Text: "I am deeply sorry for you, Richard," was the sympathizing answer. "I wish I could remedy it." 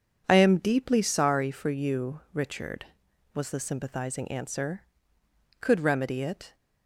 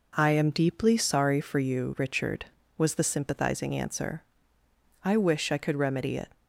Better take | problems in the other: second | skips "I wish I"; at 5.2 s

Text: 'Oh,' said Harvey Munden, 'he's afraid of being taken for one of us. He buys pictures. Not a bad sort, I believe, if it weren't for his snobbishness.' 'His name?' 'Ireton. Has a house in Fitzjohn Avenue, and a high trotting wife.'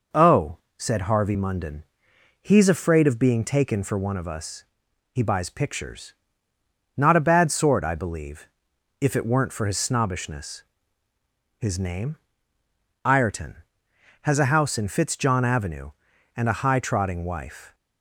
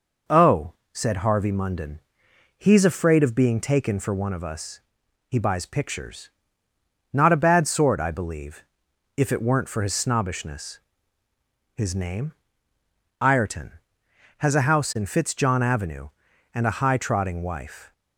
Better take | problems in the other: neither | none

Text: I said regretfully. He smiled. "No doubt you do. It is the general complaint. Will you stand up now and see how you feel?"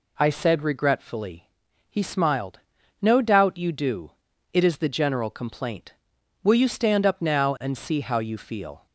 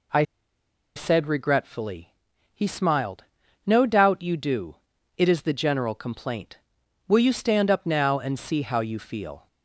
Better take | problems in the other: first | pauses between "I" and "said"; noticeable; at 0.2 s; 0.73 s long

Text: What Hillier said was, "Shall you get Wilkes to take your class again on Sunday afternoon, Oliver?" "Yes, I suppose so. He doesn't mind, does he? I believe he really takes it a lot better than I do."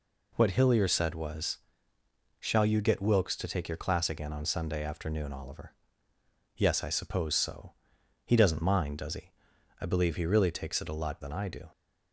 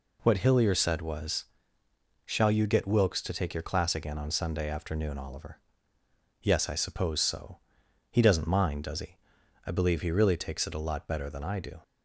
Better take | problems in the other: second | skips "better"; at 11.2 s

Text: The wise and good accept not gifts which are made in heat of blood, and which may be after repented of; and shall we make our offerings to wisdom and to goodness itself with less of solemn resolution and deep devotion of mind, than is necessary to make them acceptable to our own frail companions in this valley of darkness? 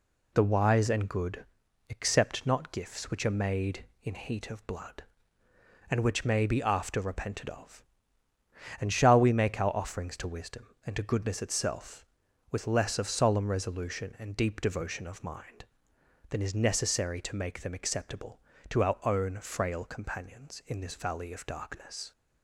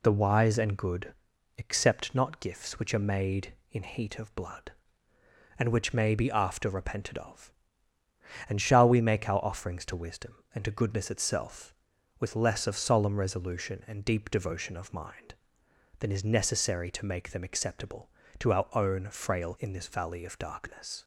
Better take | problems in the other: first | pauses between "good" and "accept"; at 1.1 s; 0.44 s long; also in the first // skips "companions"; at 19.5 s

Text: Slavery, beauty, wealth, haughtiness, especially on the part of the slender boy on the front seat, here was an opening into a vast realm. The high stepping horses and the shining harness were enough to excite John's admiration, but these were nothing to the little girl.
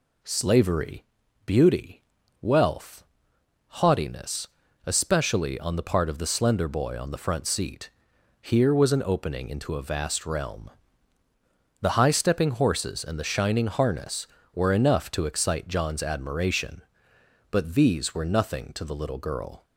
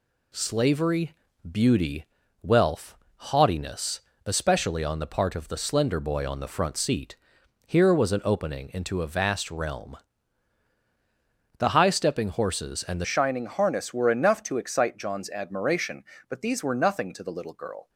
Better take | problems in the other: first | changes voice at "shining"; from 13.0 s on; 4.8 s long

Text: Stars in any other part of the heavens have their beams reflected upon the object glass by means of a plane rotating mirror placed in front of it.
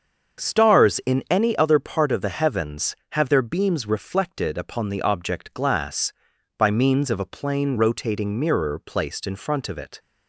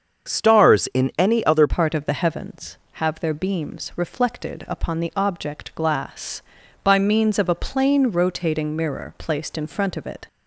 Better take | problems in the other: first | starts louder than the rest; until 1.3 s; 7 dB; also in the first // changes voice at "part"; from 1.6 s on; 8.6 s long

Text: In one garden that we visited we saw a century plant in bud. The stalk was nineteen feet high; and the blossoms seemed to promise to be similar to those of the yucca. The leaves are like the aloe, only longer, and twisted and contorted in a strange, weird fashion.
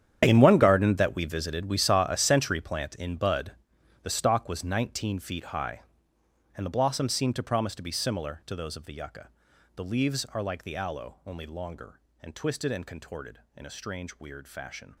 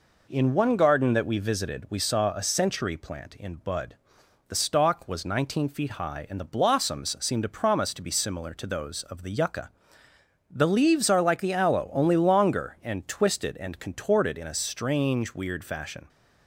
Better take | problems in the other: second | gets quieter; strong; throughout; 15.5 dB

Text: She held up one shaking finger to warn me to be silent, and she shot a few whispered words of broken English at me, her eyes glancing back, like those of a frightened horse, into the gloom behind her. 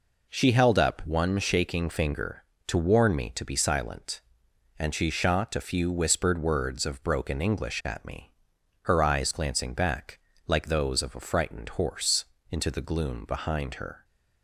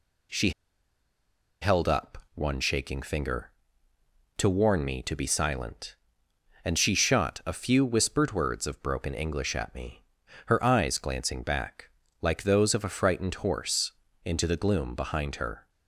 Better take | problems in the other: first | pauses between "She" and "held"; at 0.5 s; 1.1 s long // pauses between "up" and "one"; slight; at 2.1 s; 0.18 s long

